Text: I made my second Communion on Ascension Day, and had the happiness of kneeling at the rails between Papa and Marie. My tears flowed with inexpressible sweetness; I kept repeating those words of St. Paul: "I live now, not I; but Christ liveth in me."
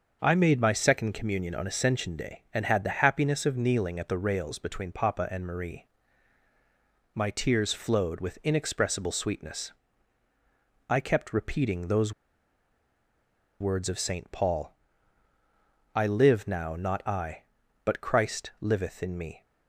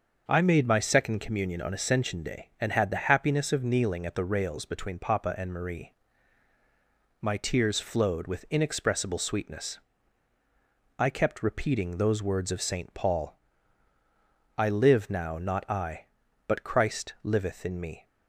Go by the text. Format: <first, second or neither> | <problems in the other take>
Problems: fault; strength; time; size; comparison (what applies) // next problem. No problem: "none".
second | starts louder than the rest; until 1.2 s; 6.5 dB; also in the second // pauses between "those" and "words"; strong; at 12.1 s; 1.4 s long